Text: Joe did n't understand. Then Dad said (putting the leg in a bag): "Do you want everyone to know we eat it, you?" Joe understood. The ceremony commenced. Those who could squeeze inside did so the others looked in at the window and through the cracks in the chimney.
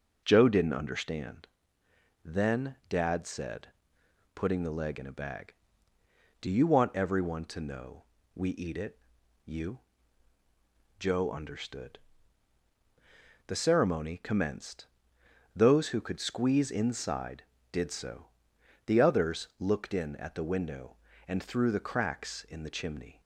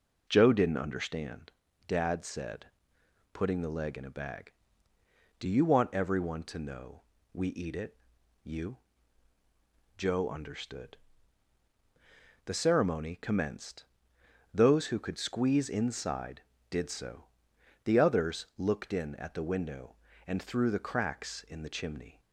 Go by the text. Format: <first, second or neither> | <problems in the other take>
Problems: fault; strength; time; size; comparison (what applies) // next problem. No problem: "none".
first | skips "Then"; at 1.6 s // pauses between "know" and "we"; slight; at 7.0 s; 0.30 s long; slight in the first // pauses between "so" and "the"; noticeable; at 17.2 s; 0.58 s long; noticeable in the first